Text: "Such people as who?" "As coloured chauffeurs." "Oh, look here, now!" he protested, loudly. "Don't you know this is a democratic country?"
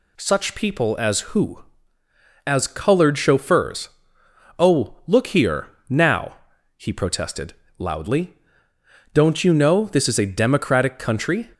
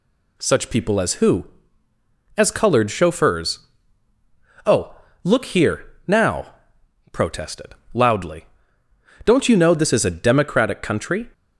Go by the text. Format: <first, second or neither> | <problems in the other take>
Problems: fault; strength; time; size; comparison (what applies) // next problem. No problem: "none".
first | skips "he"; at 6.8 s